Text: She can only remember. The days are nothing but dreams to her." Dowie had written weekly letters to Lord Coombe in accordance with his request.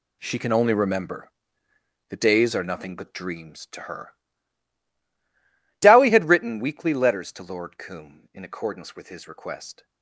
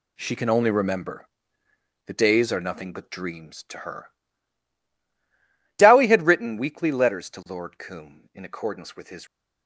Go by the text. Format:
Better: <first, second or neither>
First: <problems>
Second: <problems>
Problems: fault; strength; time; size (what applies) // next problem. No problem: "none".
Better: first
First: none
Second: stops before "request"; at 9.2 s